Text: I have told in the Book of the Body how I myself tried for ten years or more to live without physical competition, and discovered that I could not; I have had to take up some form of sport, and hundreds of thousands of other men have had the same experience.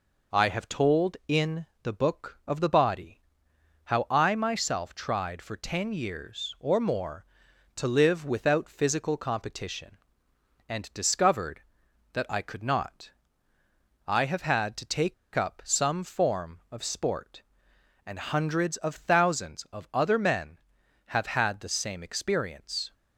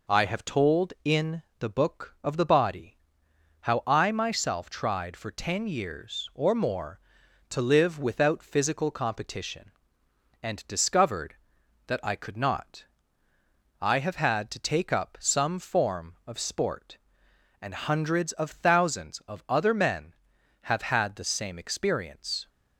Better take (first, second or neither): second